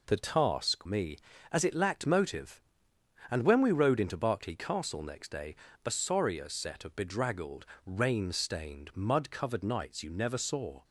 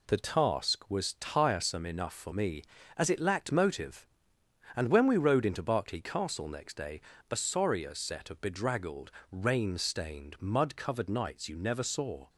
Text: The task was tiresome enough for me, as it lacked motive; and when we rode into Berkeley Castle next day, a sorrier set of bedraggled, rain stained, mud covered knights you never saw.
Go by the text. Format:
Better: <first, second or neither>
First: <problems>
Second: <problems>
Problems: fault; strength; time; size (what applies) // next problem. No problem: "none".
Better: second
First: skips "was tiresome enough for"; at 0.8 s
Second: none